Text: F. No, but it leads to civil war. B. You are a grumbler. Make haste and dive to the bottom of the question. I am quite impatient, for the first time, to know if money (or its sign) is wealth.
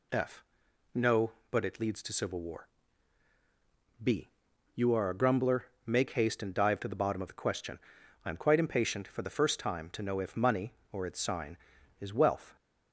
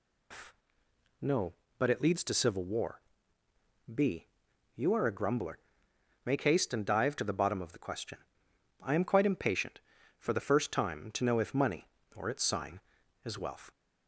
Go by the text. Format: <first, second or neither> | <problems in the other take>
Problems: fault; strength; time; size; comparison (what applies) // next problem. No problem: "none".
first | loses the start of "F"; at 0.3 s; 150 ms